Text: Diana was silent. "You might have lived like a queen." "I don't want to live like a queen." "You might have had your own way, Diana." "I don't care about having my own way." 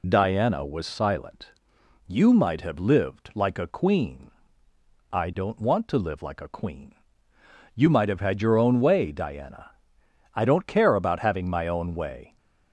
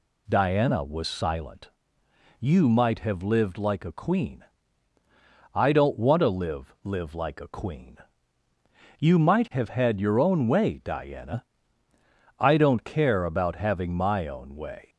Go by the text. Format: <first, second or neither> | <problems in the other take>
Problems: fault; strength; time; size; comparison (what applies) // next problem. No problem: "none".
first | says "live" twice; at 6.8 s